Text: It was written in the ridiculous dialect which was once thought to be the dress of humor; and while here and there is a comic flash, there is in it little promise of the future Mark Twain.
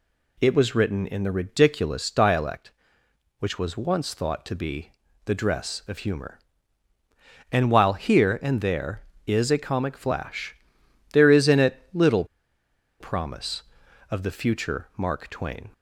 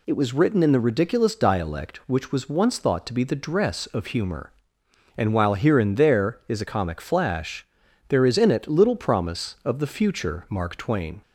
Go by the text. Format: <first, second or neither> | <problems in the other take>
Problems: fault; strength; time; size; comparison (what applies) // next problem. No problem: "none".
second | pauses between "be" and "the"; slight; at 4.9 s; 0.36 s long // pauses between "little" and "promise"; noticeable; at 12.2 s; 0.75 s long